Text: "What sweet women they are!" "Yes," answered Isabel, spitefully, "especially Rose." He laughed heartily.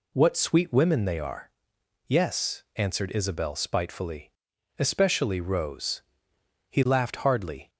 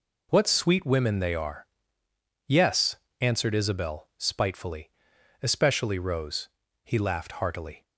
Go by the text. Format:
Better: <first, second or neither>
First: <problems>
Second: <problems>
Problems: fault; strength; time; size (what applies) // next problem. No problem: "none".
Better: second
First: says "hardly" for "heartily"; at 7.1 s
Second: none